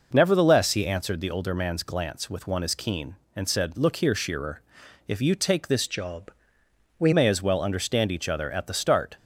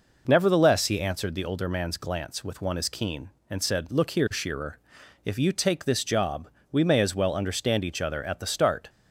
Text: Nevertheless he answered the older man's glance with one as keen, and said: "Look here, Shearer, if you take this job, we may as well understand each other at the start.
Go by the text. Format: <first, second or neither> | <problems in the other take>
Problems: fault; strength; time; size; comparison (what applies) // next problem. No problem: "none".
second | changes voice from "job" to "we"; from 5.8 to 7.1 s; 1.3 s long